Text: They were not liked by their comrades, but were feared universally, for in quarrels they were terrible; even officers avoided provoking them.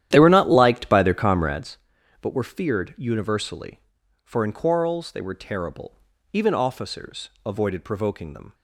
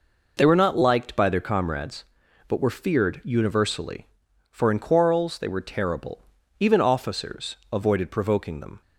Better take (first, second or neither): second